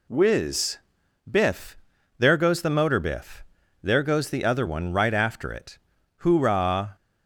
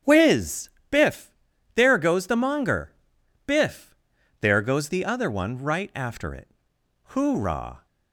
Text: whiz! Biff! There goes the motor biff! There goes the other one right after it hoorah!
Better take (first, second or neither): first